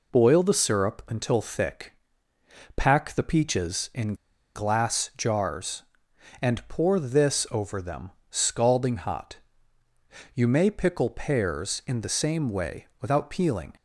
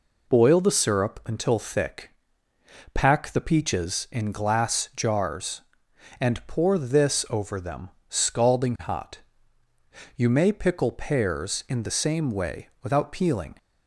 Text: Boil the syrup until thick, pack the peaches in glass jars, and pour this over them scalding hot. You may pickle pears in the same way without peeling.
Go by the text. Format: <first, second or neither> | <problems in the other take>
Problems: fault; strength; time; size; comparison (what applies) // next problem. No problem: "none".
second | pauses between "in" and "glass"; at 4.1 s; 0.39 s long // pauses between "them" and "scalding"; slight; at 8.1 s; 0.18 s long; slight in the second